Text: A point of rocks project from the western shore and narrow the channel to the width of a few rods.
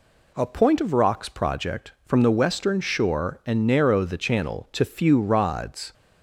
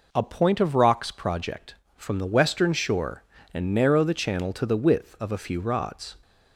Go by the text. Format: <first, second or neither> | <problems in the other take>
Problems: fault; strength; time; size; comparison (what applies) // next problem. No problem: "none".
second | skips "the width of a"; at 4.8 s